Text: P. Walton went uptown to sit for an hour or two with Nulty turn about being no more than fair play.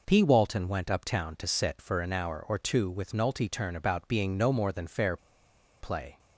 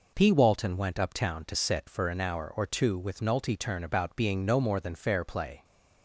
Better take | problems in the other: second | pauses between "fair" and "play"; noticeable; at 5.1 s; 0.64 s long

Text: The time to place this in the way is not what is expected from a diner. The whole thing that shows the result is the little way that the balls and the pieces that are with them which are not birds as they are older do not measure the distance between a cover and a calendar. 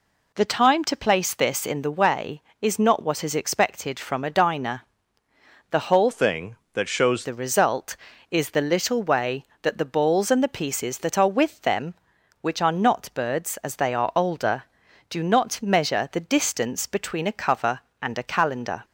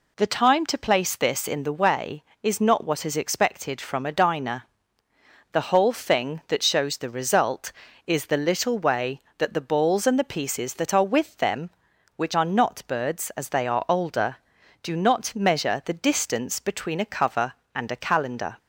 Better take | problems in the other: second | changes voice from "thing" to "shows"; from 6.1 to 7.2 s; 1.1 s long

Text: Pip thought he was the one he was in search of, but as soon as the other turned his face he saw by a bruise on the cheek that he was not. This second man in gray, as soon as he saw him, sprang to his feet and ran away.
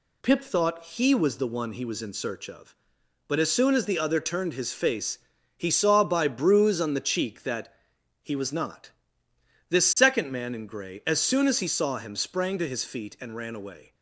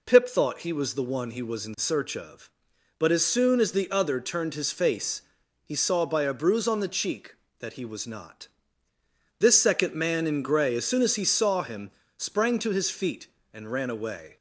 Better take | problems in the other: second | pauses between "face" and "he"; at 5.1 s; 0.40 s long; also in the second // skips "a"; at 6.2 s // pauses between "that" and "he"; noticeable; at 7.7 s; 0.50 s long

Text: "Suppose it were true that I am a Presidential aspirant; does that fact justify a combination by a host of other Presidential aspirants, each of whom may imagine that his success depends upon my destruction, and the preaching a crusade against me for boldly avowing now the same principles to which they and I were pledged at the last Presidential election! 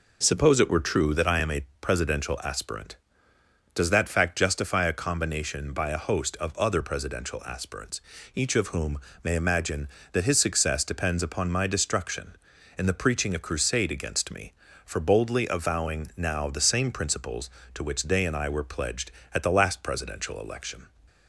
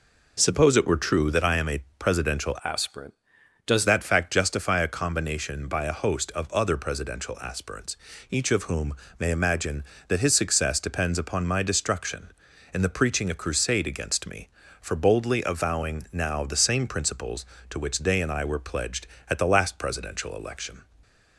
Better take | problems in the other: first | pauses between "a" and "Presidential"; slight; at 1.8 s; 0.16 s long; slight in the first // changes voice from "aspirant" to "does"; from 2.6 to 3.8 s; 1.2 s long // pauses between "whom" and "may"; slight; at 8.9 s; 0.26 s long; slight in the first

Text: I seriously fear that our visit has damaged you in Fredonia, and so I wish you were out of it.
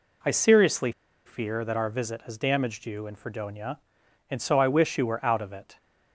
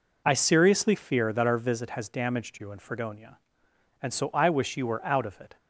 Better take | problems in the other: second | pauses between "seriously" and "fear"; slight; at 0.9 s; 0.35 s long

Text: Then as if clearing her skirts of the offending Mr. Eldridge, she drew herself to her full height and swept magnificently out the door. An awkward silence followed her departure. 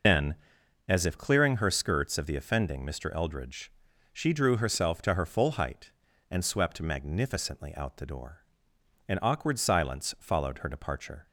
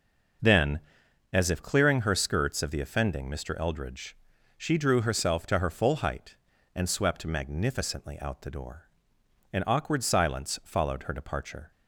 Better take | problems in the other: second | loses the start of "Then"; at 0.0 s; 100 ms

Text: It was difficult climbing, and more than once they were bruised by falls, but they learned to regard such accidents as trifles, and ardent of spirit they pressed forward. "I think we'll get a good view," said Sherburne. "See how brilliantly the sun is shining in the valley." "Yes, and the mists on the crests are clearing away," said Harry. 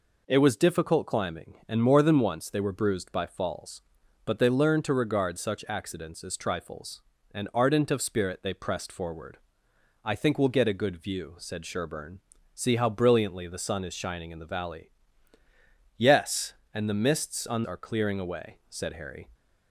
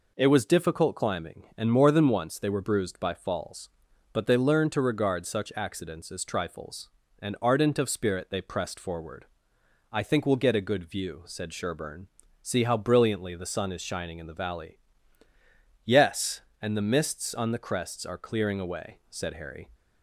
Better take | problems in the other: second | skips "the crests"; at 17.6 s

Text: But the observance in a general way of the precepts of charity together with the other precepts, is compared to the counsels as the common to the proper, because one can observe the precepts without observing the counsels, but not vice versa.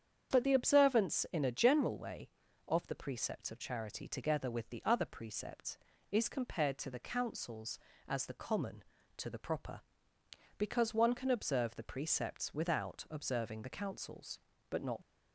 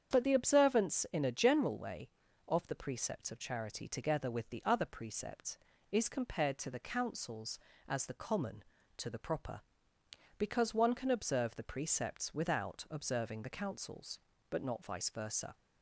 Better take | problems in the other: second | starts louder than the rest; strong; until 1.3 s; 8 dB; strong in the second // stops before "vice versa"; at 15.0 s

